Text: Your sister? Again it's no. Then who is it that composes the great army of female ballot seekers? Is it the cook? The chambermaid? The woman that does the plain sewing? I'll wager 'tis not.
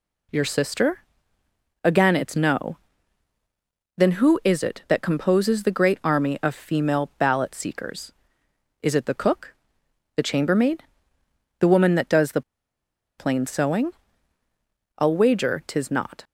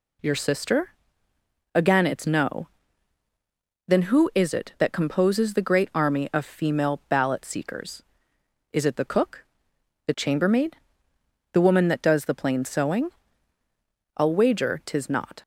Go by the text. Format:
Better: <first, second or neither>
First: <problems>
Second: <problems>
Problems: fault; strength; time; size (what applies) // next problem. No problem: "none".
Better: second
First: pauses between "the" and "plain"; noticeable; at 12.4 s; 0.75 s long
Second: none